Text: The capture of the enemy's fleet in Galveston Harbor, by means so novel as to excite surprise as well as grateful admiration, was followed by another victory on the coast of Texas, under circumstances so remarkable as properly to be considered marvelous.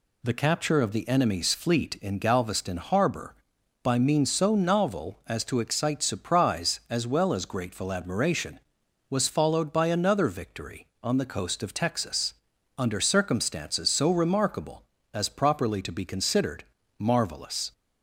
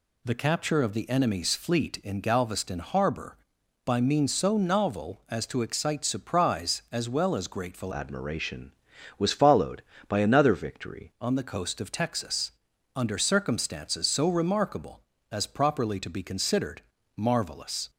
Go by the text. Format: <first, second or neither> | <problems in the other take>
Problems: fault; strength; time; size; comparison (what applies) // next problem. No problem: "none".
first | changes voice from "admiration" to "victory"; from 7.9 to 11.1 s; 3.2 s long // pauses between "considered" and "marvelous"; slight; at 16.8 s; 0.34 s long; slight in the first